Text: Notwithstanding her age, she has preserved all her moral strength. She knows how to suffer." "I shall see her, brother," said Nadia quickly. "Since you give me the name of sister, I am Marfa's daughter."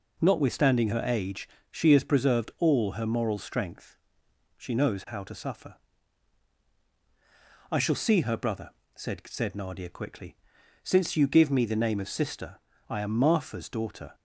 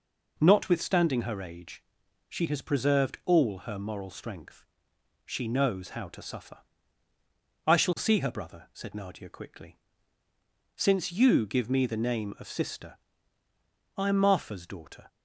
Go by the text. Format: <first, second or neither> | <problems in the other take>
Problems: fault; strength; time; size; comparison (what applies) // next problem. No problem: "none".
second | says "said" twice; at 9.2 s